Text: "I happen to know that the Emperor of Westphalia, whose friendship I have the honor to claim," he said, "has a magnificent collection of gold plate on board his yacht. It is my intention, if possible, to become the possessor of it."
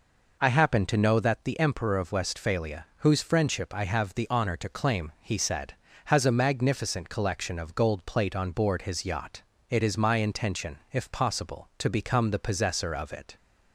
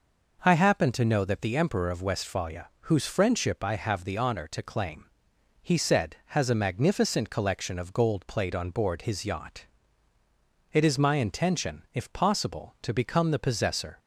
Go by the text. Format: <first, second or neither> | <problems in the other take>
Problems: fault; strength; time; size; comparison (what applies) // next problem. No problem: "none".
first | stops before "of it"; at 13.9 s